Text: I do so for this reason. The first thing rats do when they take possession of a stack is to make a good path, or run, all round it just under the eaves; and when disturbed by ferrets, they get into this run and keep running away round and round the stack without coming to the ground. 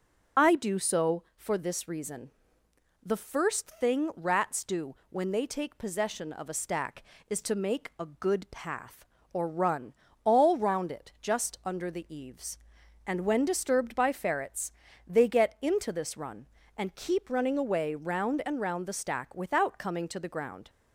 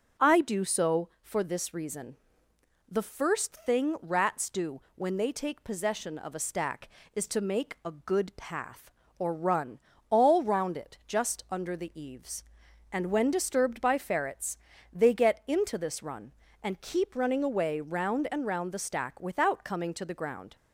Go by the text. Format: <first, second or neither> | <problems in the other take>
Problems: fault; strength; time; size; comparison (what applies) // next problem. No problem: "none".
second | loses the start of "I"; at 0.3 s; 35 ms // pauses between "do" and "when"; slight; at 4.9 s; 0.16 s long; slight in the second